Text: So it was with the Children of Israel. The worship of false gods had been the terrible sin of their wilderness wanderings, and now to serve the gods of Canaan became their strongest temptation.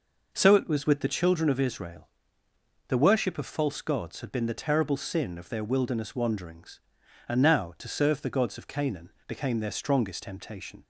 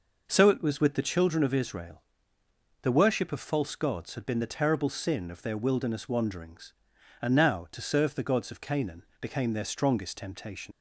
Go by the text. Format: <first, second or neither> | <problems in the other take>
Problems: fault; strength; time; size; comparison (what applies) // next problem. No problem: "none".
first | pauses between "Canaan" and "became"; slight; at 9.0 s; 0.18 s long; slight in the first // leaves "temptation" unfinished; at 10.7 s; 70 ms